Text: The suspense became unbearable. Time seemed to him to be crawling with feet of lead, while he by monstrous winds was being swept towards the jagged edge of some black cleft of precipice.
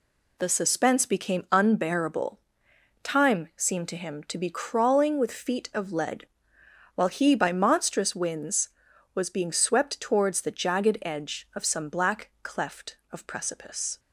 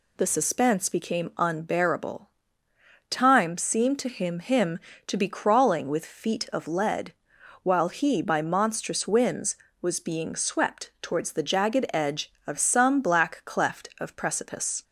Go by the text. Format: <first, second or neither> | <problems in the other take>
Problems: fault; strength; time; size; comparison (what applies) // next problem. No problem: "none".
first | says "him" twice; at 4.3 s